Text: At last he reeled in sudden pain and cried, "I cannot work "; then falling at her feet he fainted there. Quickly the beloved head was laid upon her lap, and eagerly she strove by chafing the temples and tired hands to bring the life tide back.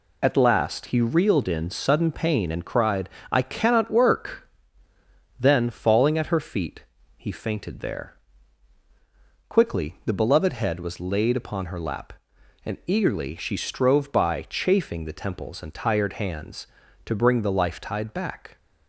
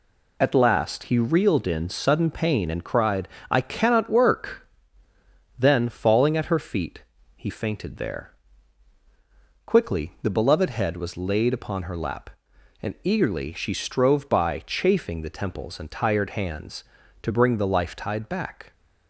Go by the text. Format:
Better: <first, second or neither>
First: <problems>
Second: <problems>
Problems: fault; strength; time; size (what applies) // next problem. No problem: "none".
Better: neither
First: pauses between "feet" and "he"; slight; at 6.8 s; 0.34 s long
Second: pauses between "feet" and "he"; slight; at 7.0 s; 0.34 s long